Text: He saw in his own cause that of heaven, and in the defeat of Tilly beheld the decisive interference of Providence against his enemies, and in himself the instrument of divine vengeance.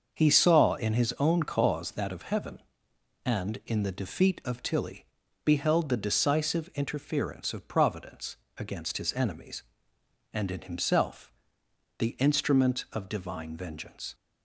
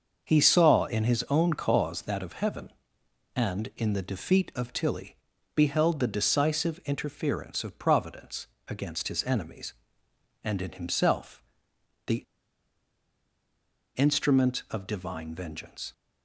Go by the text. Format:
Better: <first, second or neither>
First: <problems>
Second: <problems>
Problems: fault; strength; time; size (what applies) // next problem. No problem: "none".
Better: first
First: starts louder than the rest; until 1.1 s; 6.5 dB // pauses between "Tilly" and "beheld"; at 5.0 s; 0.38 s long // pauses between "Providence" and "against"; slight; at 8.3 s; 0.22 s long // pauses between "himself" and "the"; noticeable; at 11.3 s; 0.66 s long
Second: starts louder than the rest; until 1.2 s; 6.5 dB // pauses between "Tilly" and "beheld"; at 5.1 s; 0.38 s long // pauses between "Providence" and "against"; slight; at 8.4 s; 0.22 s long // pauses between "himself" and "the"; noticeable; at 11.4 s; 0.64 s long // pauses between "the" and "instrument"; strong; at 12.2 s; 1.7 s long